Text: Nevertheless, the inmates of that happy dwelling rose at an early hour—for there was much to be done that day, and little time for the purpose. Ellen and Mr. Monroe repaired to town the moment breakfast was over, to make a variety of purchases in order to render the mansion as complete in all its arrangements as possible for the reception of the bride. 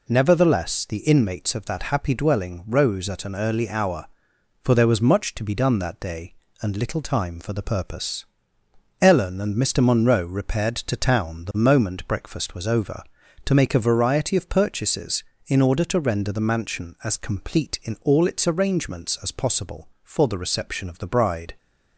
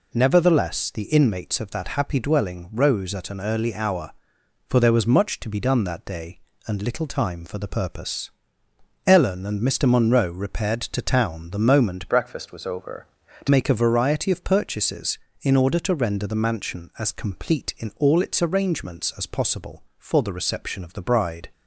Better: first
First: none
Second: changes voice from "breakfast" to "to"; from 12.0 to 13.4 s; 1.4 s long

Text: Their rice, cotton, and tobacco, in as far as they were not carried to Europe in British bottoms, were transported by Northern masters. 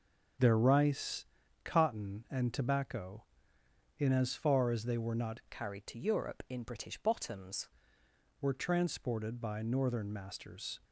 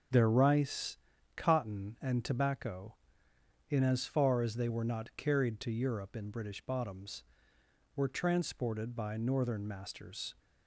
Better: second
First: starts louder than the rest; until 1.7 s; 6.5 dB // changes voice from "carried" to "bottoms"; from 5.5 to 7.6 s; 2.1 s long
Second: starts louder than the rest; until 1.4 s; 6.5 dB

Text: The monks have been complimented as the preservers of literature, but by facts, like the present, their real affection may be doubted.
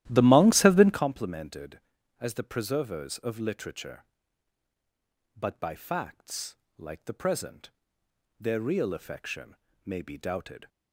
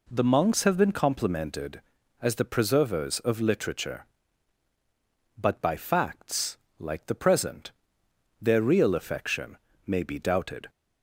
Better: second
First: starts louder than the rest; strong; until 1.1 s; 13.5 dB // pauses between "affection" and "may"; slight; at 9.5 s; 0.28 s long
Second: pauses between "affection" and "may"; slight; at 9.5 s; 0.28 s long

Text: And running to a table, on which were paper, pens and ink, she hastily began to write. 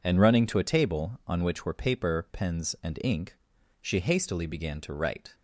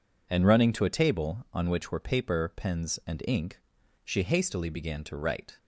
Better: neither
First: none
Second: none

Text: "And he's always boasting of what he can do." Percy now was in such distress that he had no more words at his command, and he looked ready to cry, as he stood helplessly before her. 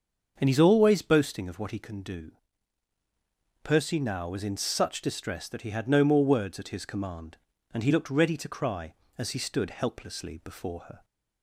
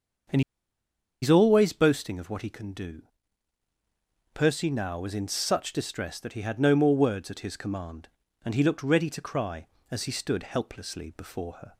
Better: first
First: starts louder than the rest; until 1.3 s; 6.5 dB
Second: starts louder than the rest; until 2.1 s; 6.5 dB // pauses between "And" and "he's"; noticeable; at 0.4 s; 0.81 s long

